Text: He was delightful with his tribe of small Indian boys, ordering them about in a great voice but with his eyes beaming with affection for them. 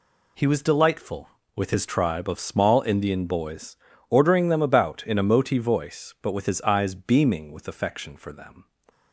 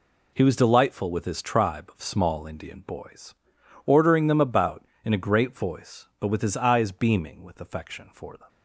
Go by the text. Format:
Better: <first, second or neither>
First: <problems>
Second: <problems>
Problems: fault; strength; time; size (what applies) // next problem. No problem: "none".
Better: second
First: says "moti" for "great"; at 5.2 s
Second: none